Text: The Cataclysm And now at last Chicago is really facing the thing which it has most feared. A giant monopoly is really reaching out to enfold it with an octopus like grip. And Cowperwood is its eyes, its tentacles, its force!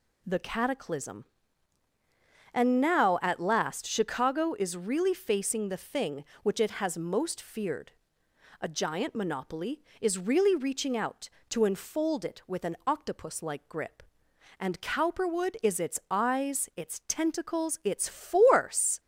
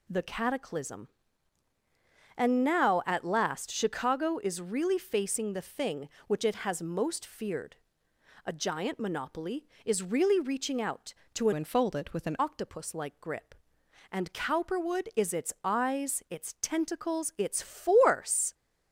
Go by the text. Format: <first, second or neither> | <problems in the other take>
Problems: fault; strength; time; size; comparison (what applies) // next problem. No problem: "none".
first | changes voice from "enfold" to "an"; from 11.5 to 12.3 s; 0.8 s long